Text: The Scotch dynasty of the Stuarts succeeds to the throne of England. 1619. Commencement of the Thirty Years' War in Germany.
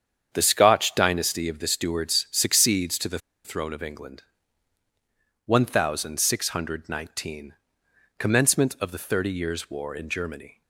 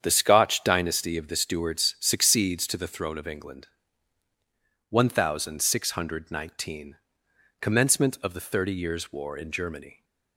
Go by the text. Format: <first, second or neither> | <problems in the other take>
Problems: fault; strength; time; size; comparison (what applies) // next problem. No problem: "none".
second | starts louder than the rest; strong; until 1.3 s; 8 dB; strong in the second // pauses between "the" and "throne"; slight; at 3.1 s; 0.27 s long